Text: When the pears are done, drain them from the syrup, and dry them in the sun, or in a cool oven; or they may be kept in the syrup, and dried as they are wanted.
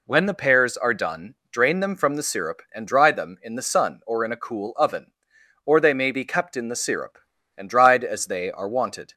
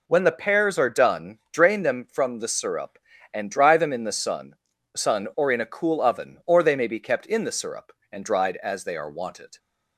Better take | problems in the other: first | says "sun" twice; at 4.9 s

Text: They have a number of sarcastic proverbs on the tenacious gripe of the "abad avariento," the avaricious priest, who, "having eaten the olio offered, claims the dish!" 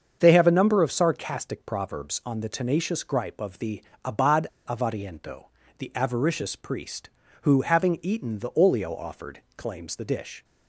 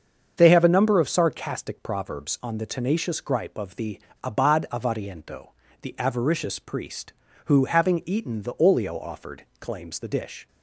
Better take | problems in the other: second | starts louder than the rest; until 1.2 s; 7 dB; also in the second // pauses between "the" and "abad"; slight; at 3.8 s; 0.20 s long; slight in the second // pauses between "abad" and "avariento"; slight; at 4.4 s; 0.19 s long

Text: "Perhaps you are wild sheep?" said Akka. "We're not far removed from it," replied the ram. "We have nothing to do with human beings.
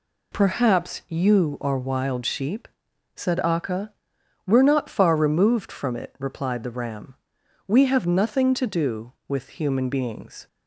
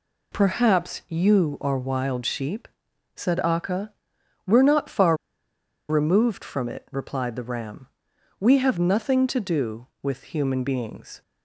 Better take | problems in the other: first | pauses between "far" and "removed"; noticeable; at 5.1 s; 0.74 s long

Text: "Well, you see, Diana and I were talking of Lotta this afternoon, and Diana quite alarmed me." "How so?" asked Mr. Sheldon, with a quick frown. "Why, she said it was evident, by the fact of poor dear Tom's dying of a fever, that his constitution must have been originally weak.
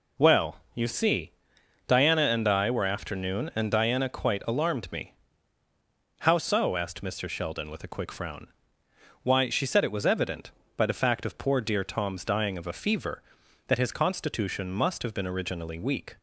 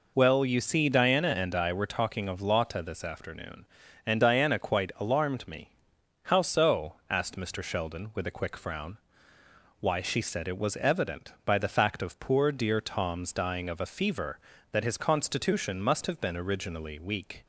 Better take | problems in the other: second | skips "talking of Lotta this"; at 2.8 s

